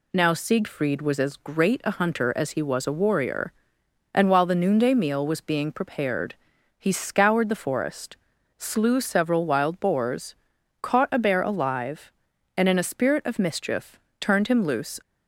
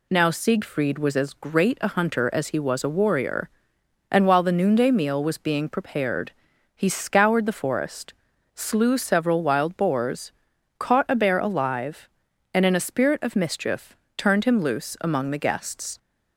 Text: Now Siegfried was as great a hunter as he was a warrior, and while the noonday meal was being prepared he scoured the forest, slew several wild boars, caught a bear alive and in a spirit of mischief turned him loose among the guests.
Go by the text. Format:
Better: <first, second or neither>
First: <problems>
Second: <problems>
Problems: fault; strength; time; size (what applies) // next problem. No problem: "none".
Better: second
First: pauses between "prepared" and "he"; noticeable; at 6.3 s; 0.46 s long // pauses between "mischief" and "turned"; slight; at 13.9 s; 0.20 s long // stops before "among the guests"; at 15.0 s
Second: pauses between "prepared" and "he"; noticeable; at 6.3 s; 0.46 s long // pauses between "mischief" and "turned"; slight; at 13.9 s; 0.20 s long